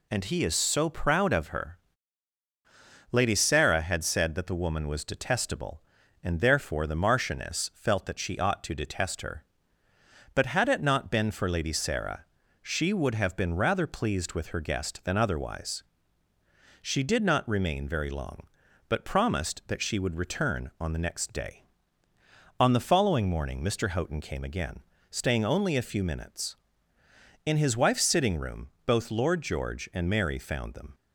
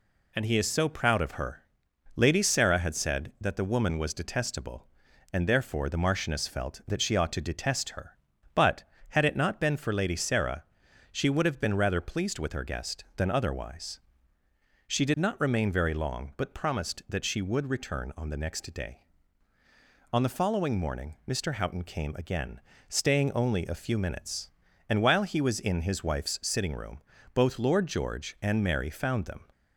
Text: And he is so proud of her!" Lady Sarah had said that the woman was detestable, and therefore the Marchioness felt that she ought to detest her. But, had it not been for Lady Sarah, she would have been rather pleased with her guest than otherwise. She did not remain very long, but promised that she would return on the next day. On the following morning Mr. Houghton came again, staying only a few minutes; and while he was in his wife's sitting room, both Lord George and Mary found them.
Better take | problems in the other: second | skips "and while he was"; at 26.9 s

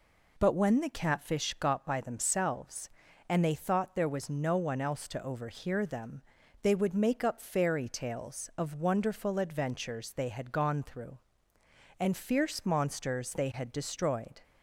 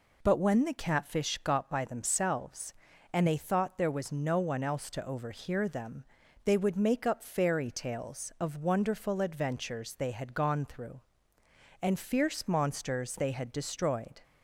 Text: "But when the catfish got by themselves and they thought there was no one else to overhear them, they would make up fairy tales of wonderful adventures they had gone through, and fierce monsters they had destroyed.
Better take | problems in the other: neither | none

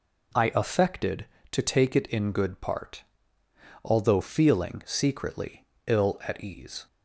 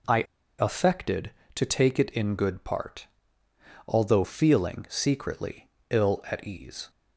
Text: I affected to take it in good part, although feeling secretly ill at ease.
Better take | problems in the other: first | pauses between "I" and "affected"; at 0.2 s; 0.36 s long // pauses between "secretly" and "ill"; slight; at 5.6 s; 0.22 s long; slight in the first

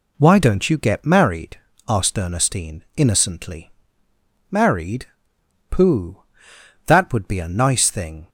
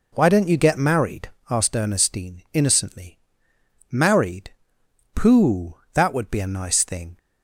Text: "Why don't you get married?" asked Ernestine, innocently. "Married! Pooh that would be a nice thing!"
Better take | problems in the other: first | starts louder than the rest; noticeable; until 1.5 s; 4 dB

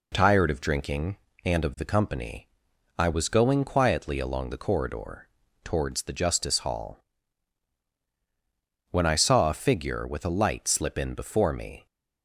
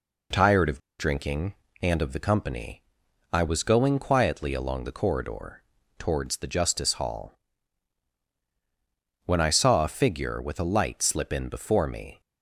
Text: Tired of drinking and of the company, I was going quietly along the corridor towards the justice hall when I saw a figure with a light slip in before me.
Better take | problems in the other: first | pauses between "of" and "drinking"; slight; at 0.7 s; 0.19 s long // pauses between "corridor" and "towards"; slight; at 5.6 s; 0.34 s long; slight in the first // pauses between "hall" and "when"; strong; at 7.3 s; 1.9 s long; strong in the first

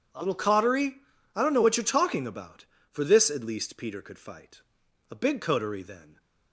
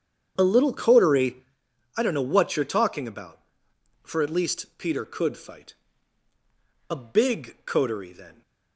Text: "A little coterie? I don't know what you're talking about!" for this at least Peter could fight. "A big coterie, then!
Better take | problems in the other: first | starts louder than the rest; strong; until 1.3 s; 8 dB // skips "this"; at 4.2 s

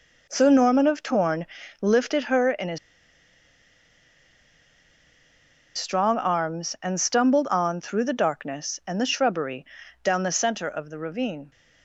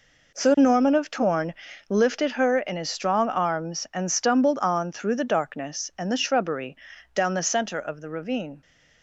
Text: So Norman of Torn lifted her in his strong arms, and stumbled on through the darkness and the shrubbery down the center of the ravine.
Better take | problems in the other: second | pauses between "Torn" and "lifted"; slight; at 1.4 s; 0.34 s long; slight in the second // pauses between "his" and "strong"; strong; at 2.7 s; 2.9 s long // pauses between "shrubbery" and "down"; at 9.6 s; 0.38 s long; also in the second

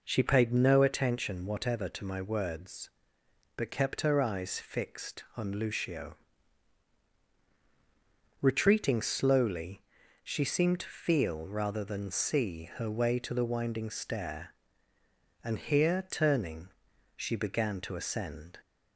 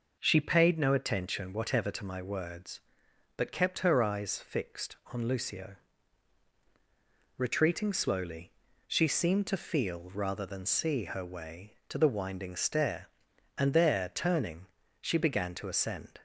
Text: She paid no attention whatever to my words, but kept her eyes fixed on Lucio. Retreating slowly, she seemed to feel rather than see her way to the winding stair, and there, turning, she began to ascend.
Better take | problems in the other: second | says "here" for "there"; at 15.5 s

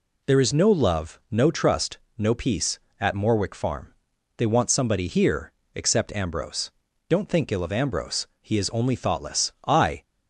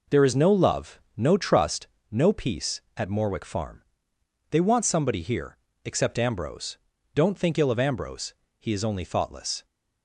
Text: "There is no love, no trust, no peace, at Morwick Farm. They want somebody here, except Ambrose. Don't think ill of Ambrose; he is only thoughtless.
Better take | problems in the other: second | goes on to say "I"; slight; from 9.6 s on; 0.36 s long

